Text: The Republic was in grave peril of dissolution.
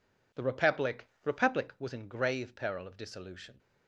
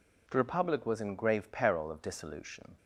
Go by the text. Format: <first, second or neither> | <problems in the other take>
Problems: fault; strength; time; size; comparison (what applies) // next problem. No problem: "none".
second | says "Republic" twice; at 1.2 s